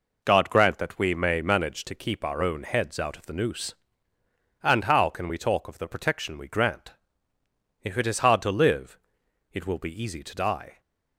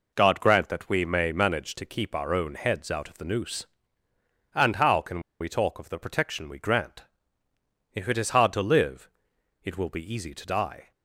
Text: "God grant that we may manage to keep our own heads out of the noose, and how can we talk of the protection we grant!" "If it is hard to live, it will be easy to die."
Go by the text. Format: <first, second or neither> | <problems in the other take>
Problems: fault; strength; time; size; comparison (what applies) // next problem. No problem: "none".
first | pauses between "can" and "we"; slight; at 5.2 s; 0.19 s long